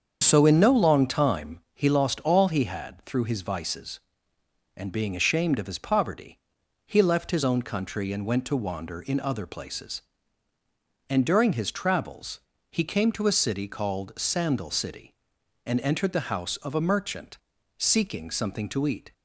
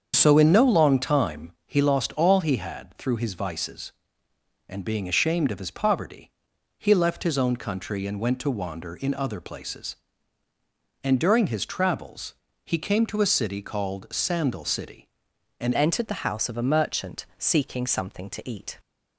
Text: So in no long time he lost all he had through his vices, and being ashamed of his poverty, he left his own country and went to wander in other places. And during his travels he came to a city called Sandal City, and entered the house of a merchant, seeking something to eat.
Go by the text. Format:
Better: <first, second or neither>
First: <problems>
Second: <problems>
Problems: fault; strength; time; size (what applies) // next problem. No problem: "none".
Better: first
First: starts louder than the rest; strong; until 1.2 s; 7.5 dB // pauses between "time" and "he"; slight; at 1.5 s; 0.16 s long // pauses between "travels" and "he"; slight; at 12.3 s; 0.32 s long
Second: starts louder than the rest; strong; until 1.1 s; 7 dB // pauses between "time" and "he"; slight; at 1.5 s; 0.16 s long // pauses between "travels" and "he"; slight; at 12.3 s; 0.32 s long // changes voice at "entered"; from 15.7 s on; 3.0 s long